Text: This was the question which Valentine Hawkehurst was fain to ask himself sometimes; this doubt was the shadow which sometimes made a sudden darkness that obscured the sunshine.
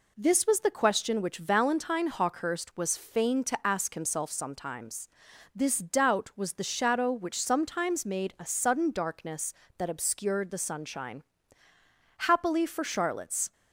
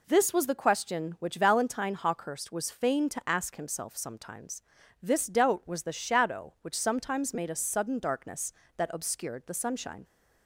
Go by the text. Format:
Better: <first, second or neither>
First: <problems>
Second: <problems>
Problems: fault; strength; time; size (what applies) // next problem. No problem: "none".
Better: second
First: goes on to say "Happily for Charlotte's"; from 12.1 s on; 1.3 s long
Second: none